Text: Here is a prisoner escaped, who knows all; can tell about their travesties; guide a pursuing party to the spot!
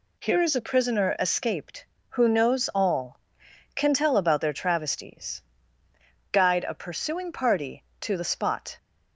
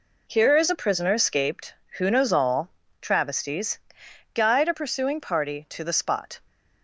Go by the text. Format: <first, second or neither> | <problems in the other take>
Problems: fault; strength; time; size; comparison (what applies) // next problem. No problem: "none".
first | skips "can tell about their"; at 2.8 s